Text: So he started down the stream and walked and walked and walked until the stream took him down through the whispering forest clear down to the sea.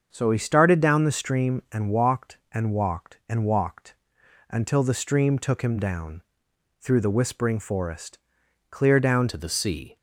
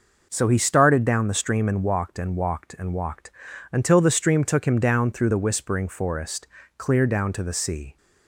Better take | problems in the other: second | starts louder than the rest; until 1.1 s; 6.5 dB // pauses between "walked" and "until"; noticeable; at 3.9 s; 0.54 s long; also in the second // pauses between "down" and "through"; noticeable; at 6.2 s; 0.60 s long // pauses between "forest" and "clear"; noticeable; at 8.1 s; 0.52 s long; slight in the second // changes voice at "to"; from 9.2 s on; 0.7 s long

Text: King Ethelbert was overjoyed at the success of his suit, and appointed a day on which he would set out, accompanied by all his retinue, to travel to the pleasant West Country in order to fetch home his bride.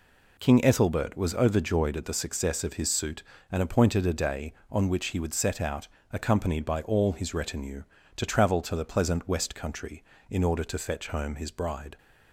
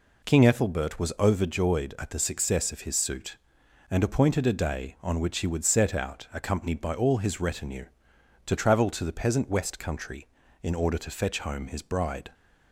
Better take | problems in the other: first | says "peasant" for "pleasant"; at 9.1 s

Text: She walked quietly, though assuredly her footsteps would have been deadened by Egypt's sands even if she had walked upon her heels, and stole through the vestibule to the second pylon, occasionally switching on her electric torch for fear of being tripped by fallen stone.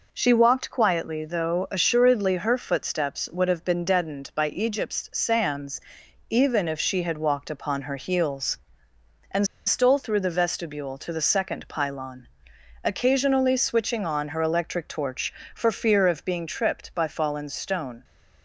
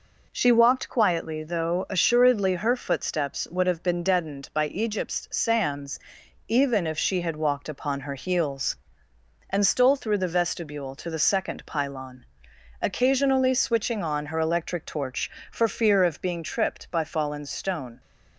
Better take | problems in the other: second | pauses between "sands" and "even"; noticeable; at 5.7 s; 0.48 s long; noticeable in the second // pauses between "and" and "stole"; slight; at 9.4 s; 0.20 s long

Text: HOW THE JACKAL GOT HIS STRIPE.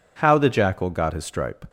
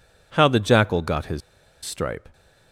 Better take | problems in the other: first | pauses between "HIS" and "STRIPE"; at 1.4 s; 0.44 s long

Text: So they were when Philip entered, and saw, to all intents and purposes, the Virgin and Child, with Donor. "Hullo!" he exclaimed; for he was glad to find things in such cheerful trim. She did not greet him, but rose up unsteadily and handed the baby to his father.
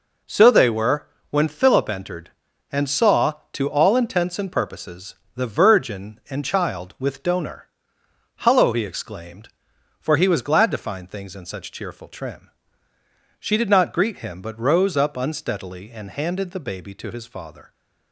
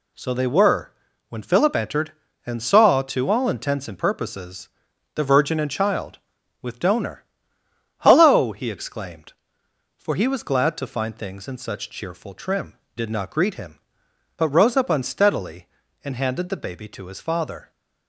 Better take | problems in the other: first | pauses between "were" and "when"; slight; at 0.9 s; 0.36 s long; slight in the first // skips "She"; at 12.8 s

